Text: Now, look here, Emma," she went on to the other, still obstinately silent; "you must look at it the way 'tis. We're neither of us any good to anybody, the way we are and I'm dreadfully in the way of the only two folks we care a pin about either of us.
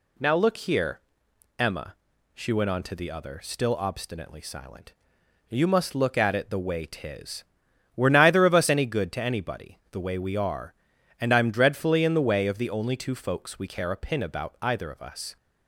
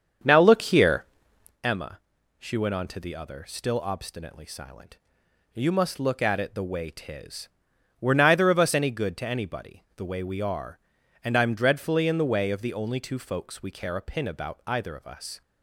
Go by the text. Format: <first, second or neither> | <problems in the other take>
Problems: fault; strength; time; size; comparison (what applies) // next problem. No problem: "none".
first | starts louder than the rest; strong; until 1.6 s; 7 dB